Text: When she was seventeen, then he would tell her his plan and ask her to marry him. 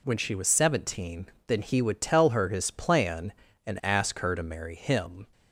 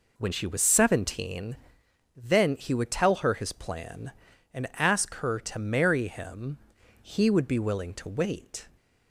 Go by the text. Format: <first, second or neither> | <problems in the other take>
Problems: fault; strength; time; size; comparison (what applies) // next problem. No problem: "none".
first | goes on to say "He would be willing to wait"; strong; from 6.9 s on; 1.6 s long